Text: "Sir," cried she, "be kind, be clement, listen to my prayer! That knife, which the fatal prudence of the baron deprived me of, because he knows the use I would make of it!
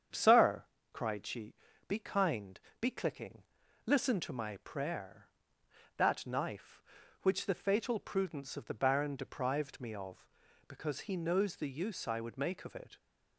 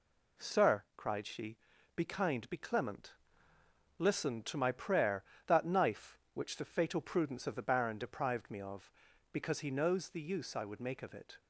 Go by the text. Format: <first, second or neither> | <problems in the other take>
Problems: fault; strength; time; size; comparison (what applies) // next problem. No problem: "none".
second | starts louder than the rest; strong; until 1.4 s; 8 dB // says "clicking" for "clement"; at 2.8 s